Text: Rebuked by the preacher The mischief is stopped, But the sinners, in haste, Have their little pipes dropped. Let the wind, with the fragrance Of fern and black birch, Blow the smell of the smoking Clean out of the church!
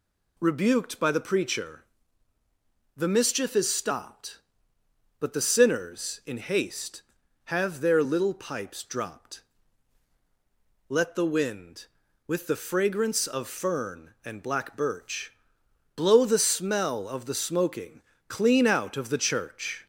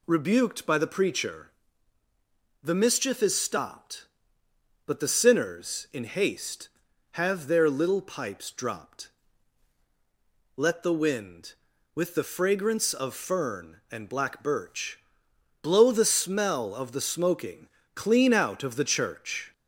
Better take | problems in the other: neither | pauses between "preacher" and "The"; the same in both // pauses between "smoking" and "Clean"; slight; the same in both

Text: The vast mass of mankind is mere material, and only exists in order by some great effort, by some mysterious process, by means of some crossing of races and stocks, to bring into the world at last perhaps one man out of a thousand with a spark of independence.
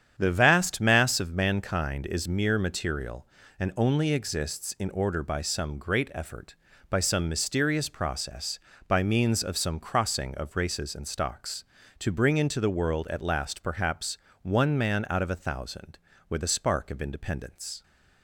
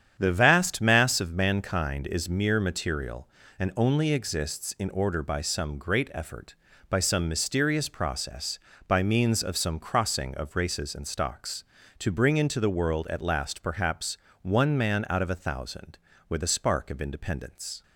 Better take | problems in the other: neither | starts louder than the rest; strong; the same in both // pauses between "perhaps" and "one"; slight; the same in both

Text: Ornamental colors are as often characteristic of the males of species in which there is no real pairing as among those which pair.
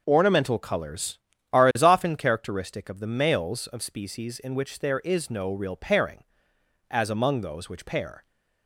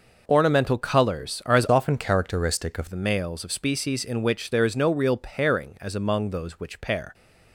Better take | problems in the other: first | changes voice from "often" to "of"; from 1.6 to 2.8 s; 1.2 s long

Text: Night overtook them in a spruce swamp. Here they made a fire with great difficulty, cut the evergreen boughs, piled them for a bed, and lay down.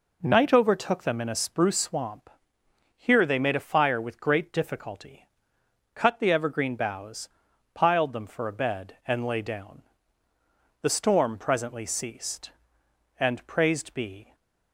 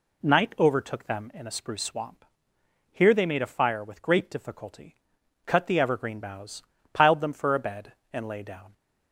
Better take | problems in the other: second | goes on to say "The storm presently ceased and praised be"; strong; from 10.8 s on; 3.5 s long

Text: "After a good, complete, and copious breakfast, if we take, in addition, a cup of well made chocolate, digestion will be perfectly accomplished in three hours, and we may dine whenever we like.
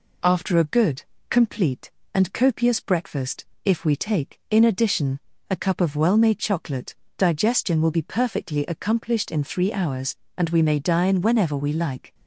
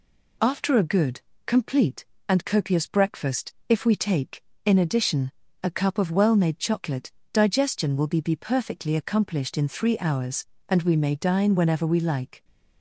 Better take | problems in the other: first | says "be" twice; at 8.2 s

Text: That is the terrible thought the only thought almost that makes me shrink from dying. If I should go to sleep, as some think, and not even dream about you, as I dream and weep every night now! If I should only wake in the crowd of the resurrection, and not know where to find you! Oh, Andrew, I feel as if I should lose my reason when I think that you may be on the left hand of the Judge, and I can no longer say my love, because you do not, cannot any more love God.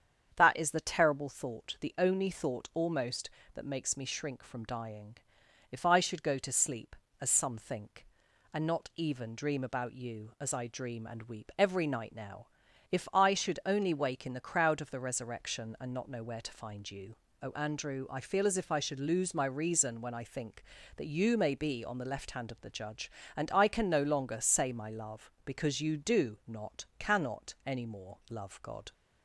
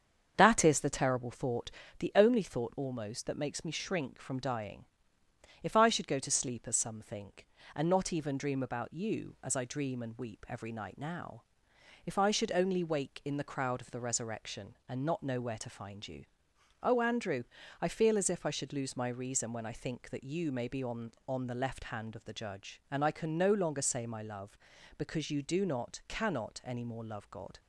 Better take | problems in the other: first | starts louder than the rest; strong; until 1.3 s; 7.5 dB; strong in the first // pauses between "thought" and "the"; slight; at 1.6 s; 0.30 s long // says "on" twice; at 21.2 s

